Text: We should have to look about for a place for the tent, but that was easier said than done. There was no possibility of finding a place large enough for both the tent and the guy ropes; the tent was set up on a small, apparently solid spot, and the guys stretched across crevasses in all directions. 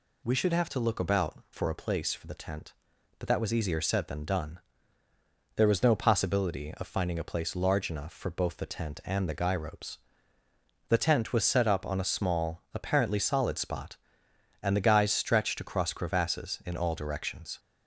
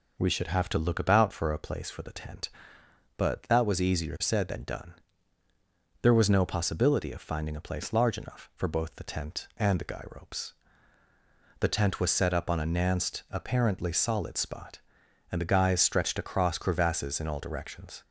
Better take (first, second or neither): first